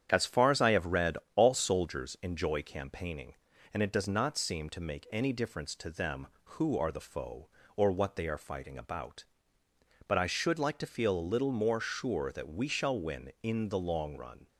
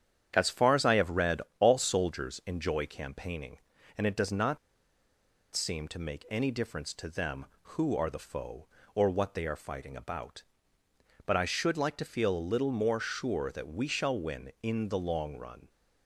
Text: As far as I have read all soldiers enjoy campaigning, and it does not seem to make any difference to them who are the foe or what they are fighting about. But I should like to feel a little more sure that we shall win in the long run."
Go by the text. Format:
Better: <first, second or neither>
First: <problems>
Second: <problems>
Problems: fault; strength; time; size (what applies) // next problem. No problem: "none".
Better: first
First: starts louder than the rest; strong; until 1.1 s; 8 dB // pauses between "read" and "all"; slight; at 1.1 s; 0.18 s long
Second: starts louder than the rest; strong; until 1.3 s; 8 dB // pauses between "read" and "all"; slight; at 1.4 s; 0.18 s long // pauses between "not" and "seem"; noticeable; at 4.5 s; 0.96 s long